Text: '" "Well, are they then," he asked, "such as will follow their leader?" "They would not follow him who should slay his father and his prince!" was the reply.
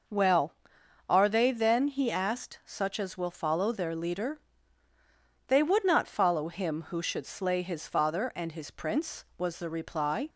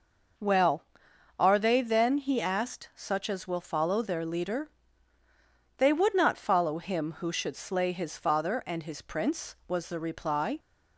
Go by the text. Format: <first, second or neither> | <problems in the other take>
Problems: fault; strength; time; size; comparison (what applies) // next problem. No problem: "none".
neither | none